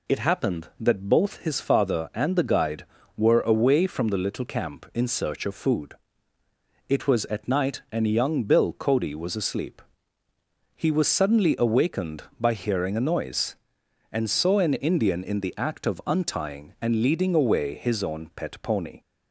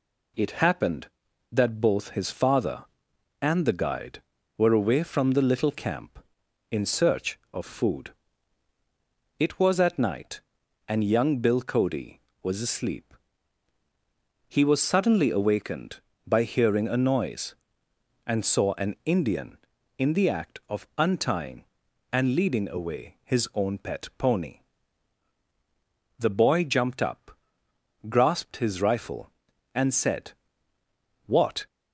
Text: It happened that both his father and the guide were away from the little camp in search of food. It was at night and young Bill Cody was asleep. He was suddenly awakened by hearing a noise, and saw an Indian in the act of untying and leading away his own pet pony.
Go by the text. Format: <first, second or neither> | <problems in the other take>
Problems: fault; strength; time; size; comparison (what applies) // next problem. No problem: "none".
first | goes on to say "The boy jumped up grasped his rifle and said What"; strong; from 26.1 s on; 5.4 s long